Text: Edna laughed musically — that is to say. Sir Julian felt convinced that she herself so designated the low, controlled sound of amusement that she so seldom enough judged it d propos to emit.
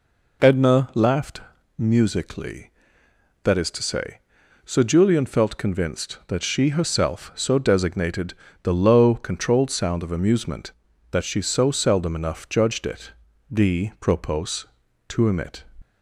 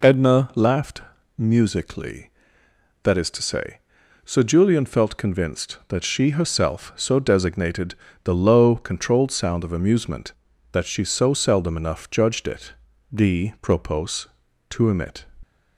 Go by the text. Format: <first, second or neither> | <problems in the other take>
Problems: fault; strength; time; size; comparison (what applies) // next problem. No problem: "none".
neither | pauses between "laughed" and "musically"; slight; the same in both // pauses between "designated" and "the"; slight; the same in both // pauses between "it" and "d"; the same in both